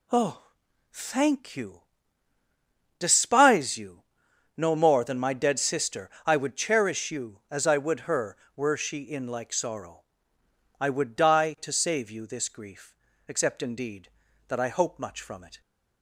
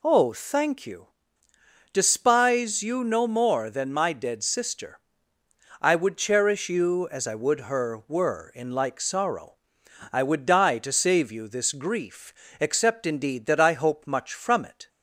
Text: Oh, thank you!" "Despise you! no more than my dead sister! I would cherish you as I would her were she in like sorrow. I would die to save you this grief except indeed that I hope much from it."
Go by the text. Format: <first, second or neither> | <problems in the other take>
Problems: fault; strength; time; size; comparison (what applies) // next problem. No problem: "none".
first | skips "she"; at 8.5 s // pauses between "grief" and "except"; slight; at 12.3 s; 0.28 s long; slight in the first